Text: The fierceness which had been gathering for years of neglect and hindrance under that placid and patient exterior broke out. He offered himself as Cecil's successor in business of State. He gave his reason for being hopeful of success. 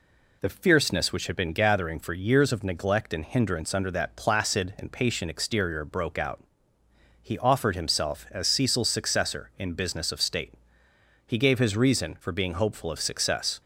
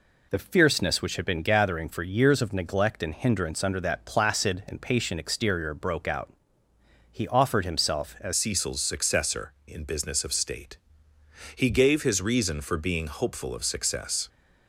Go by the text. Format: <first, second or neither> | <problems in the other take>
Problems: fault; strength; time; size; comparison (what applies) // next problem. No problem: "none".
first | changes voice at "Cecil's"; from 8.3 s on; 5.9 s long